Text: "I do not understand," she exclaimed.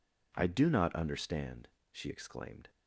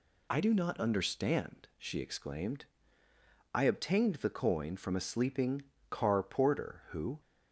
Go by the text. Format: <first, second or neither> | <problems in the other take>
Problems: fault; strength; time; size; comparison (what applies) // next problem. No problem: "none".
first | goes on to say "I obtained the coin from a sleeping car porter who"; strong; from 3.5 s on; 3.6 s long